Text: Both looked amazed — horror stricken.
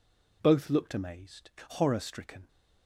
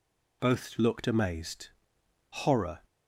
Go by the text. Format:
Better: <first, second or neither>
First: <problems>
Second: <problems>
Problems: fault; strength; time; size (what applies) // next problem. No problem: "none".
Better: first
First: none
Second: stops before "stricken"; at 2.8 s